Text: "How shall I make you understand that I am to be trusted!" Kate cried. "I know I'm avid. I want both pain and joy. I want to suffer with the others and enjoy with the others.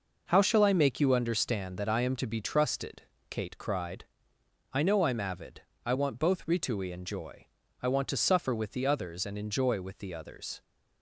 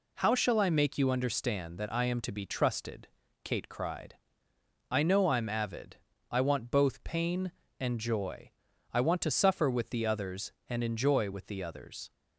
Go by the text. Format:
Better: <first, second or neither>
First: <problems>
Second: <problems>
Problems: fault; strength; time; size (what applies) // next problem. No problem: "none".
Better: second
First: says "ritui" for "pain"; at 6.4 s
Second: none